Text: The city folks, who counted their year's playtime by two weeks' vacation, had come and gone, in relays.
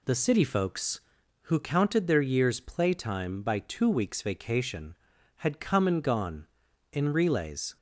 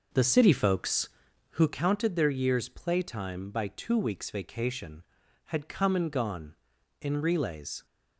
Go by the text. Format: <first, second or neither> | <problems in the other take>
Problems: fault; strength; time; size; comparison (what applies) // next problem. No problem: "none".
first | starts louder than the rest; noticeable; until 1.8 s; 5.5 dB